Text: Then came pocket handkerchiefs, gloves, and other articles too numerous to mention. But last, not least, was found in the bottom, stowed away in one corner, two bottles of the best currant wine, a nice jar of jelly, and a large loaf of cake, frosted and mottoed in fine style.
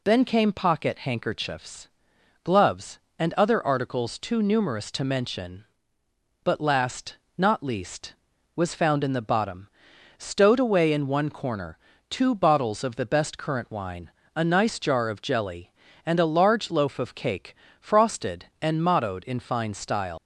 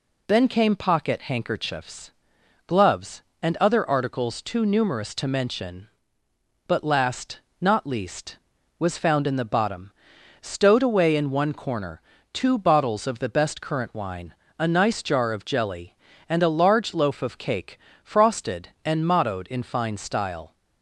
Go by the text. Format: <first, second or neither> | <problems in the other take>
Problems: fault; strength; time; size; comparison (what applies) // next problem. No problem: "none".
second | leaves "style" unfinished; at 20.1 s; 125 ms